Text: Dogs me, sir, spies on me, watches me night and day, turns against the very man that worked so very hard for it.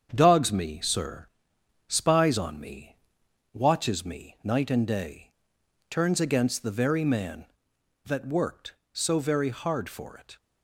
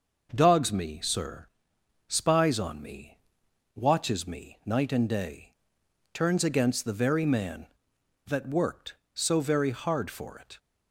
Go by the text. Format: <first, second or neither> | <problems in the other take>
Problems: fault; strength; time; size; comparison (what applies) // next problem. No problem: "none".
second | gets quieter; noticeable; throughout; 4.5 dB